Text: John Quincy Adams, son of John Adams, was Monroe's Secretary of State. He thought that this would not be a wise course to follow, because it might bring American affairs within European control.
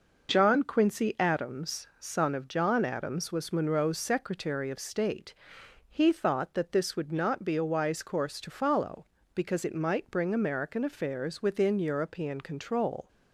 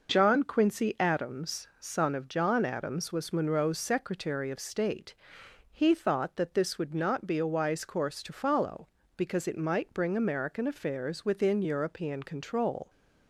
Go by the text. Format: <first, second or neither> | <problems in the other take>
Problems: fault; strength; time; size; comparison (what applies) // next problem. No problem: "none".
neither | none